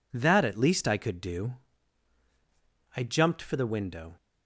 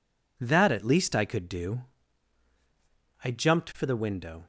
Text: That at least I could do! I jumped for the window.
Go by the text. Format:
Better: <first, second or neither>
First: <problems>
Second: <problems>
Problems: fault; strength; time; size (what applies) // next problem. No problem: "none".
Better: neither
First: none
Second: none